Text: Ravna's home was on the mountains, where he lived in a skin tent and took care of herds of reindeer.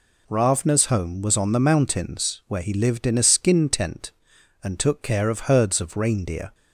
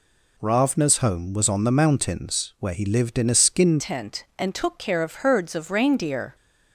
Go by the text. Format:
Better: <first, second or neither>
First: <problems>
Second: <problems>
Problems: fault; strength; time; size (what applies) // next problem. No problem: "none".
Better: first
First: none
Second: changes voice at "tent"; from 3.7 s on; 2.6 s long